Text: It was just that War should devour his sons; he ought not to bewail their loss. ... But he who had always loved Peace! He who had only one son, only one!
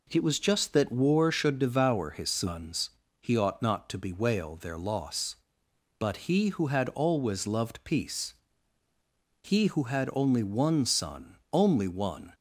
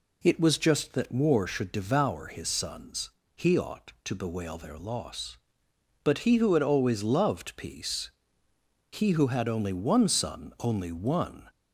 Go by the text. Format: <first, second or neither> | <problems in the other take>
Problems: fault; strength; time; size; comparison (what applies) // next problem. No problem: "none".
first | skips "not"; at 3.9 s